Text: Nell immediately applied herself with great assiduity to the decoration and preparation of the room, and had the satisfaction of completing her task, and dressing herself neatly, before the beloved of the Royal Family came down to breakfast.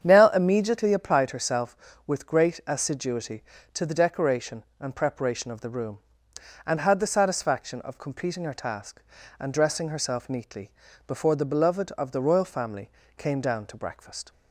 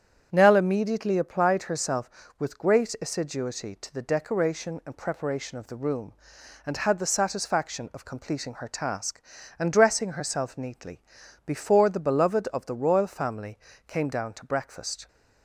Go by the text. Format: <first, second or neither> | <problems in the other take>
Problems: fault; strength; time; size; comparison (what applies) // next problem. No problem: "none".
neither | starts louder than the rest; strong; the same in both // pauses between "Family" and "came"; slight; the same in both